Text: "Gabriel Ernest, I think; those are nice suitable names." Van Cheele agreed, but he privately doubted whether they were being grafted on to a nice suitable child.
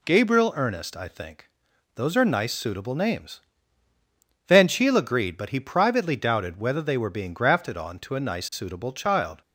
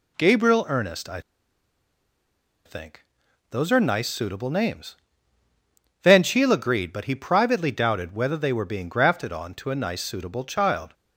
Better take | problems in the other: first | pauses between "I" and "think"; strong; at 1.2 s; 1.4 s long

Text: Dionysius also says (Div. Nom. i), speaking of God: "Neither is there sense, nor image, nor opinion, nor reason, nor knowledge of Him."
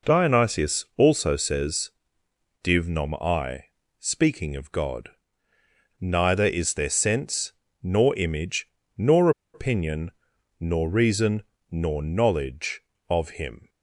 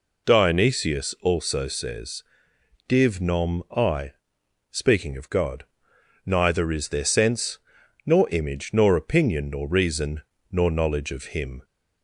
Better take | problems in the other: second | pauses between "nor" and "opinion"; slight; at 9.3 s; 0.23 s long

